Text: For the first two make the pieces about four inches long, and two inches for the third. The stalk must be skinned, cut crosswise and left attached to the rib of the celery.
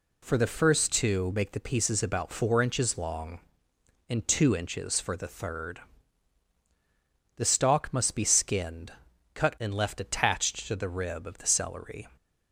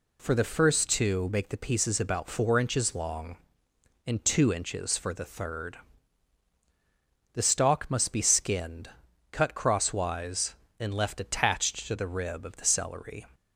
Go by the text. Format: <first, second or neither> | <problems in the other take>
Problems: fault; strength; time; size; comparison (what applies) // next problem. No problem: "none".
second | skips "crosswise"; at 9.5 s